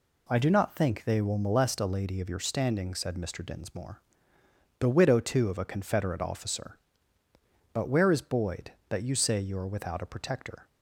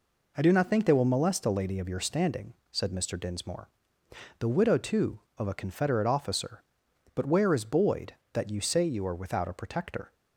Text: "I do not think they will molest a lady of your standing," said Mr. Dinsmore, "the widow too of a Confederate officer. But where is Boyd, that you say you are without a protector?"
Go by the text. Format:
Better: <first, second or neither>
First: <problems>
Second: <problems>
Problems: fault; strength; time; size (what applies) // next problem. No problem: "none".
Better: neither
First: none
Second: none